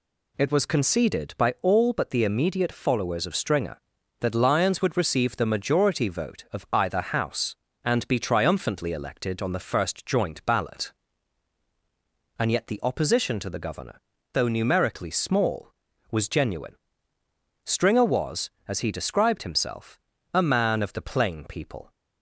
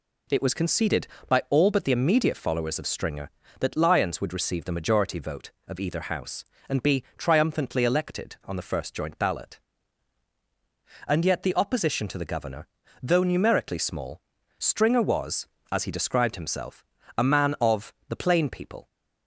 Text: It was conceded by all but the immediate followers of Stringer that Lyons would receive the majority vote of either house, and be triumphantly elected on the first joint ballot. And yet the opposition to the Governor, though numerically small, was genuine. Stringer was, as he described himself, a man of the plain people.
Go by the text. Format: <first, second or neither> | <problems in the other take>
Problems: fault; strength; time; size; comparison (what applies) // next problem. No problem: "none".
first | skips "was genuine"; at 14.3 s // pauses between "of" and "the"; slight; at 17.9 s; 0.18 s long